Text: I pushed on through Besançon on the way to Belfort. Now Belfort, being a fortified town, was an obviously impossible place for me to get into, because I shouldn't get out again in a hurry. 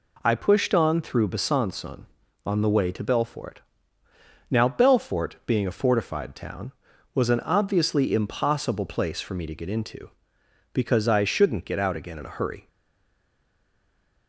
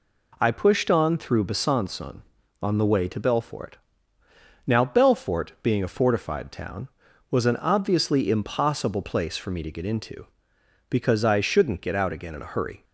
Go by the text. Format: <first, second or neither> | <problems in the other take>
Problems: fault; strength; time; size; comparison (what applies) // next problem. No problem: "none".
second | stays silent after the last word; noticeable; from 12.6 s on; 1.6 s long